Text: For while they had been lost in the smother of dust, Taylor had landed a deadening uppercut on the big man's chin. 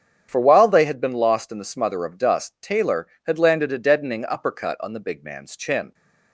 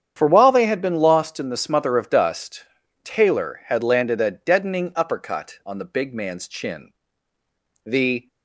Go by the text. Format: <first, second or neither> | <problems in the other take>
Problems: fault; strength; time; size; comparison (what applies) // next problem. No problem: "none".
first | starts louder than the rest; strong; until 1.1 s; 8.5 dB; strong in the first // goes on to say "The"; slight; from 7.8 s on; 0.42 s long